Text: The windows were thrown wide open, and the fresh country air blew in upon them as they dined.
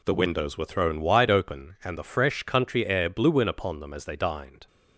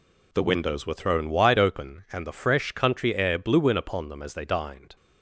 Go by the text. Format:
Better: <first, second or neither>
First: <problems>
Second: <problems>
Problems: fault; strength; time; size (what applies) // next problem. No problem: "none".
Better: neither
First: none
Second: none